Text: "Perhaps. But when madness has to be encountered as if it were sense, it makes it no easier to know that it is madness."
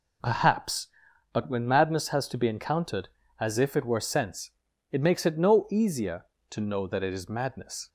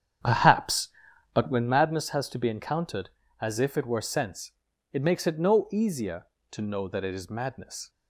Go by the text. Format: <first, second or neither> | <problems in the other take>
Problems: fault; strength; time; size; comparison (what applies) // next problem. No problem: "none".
first | starts louder than the rest; strong; until 1.8 s; 8.5 dB